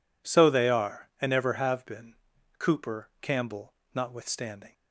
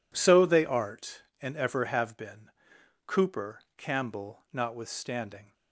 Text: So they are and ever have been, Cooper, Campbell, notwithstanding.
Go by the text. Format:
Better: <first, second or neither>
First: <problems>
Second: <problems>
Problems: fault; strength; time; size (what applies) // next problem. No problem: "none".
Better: first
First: none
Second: says "art" for "are"; at 0.6 s